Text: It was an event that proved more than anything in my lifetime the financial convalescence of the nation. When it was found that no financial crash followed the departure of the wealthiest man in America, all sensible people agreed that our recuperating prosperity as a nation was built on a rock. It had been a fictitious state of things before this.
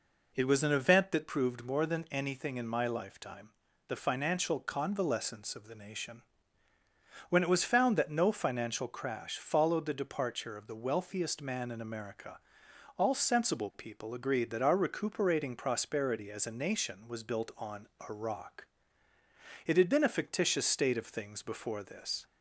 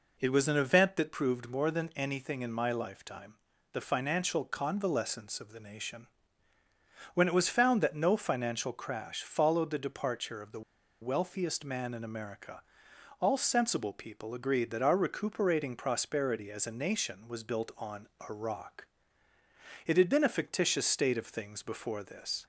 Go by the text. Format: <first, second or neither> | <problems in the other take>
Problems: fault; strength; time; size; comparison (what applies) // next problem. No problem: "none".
first | pauses between "lifetime" and "the"; at 3.3 s; 0.38 s long; also in the first // pauses between "the" and "wealthiest"; at 10.6 s; 0.40 s long // pauses between "on" and "a"; slight; at 18.0 s; 0.24 s long; slight in the first